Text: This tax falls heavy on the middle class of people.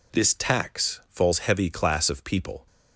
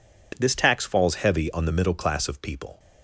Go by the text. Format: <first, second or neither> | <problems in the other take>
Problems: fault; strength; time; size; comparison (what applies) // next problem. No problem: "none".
second | skips "on the middle"; at 1.6 s